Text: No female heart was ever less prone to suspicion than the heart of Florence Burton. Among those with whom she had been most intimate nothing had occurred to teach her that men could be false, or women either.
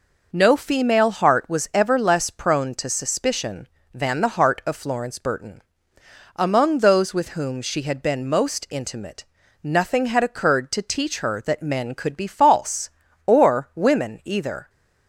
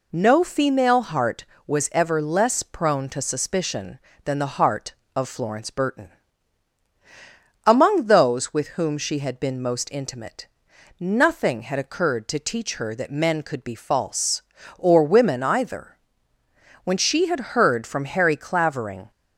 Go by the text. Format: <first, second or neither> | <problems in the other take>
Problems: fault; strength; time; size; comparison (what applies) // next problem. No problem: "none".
first | pauses between "intimate" and "nothing"; noticeable; at 10.4 s; 0.56 s long; also in the first // goes on to say "When she had heard from Harry Clavering"; strong; from 16.8 s on; 2.2 s long